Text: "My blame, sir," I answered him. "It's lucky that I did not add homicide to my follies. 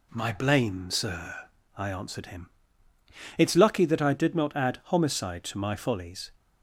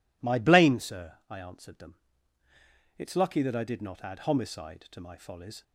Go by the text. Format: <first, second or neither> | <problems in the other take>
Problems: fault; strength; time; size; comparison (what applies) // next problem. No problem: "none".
first | says "them" for "him"; at 1.7 s